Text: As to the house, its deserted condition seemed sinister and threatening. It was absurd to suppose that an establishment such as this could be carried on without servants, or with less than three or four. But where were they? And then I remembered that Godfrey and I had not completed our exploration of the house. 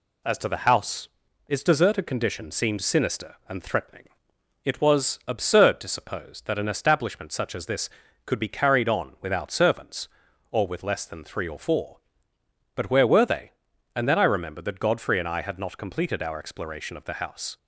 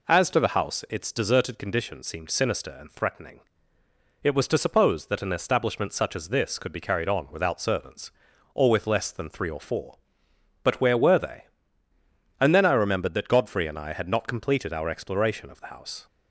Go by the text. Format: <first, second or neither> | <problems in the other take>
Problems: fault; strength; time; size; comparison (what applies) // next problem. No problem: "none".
first | skips "absurd"; at 4.4 s